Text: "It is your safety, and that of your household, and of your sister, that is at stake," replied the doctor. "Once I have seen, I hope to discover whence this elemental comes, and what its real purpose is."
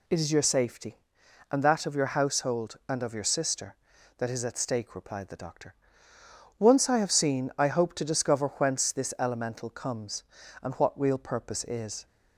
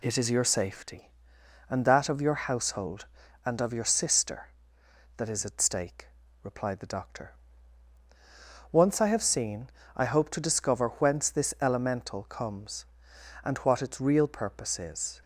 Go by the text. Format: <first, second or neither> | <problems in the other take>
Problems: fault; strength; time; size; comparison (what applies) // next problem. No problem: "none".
second | skips "its"; at 10.9 s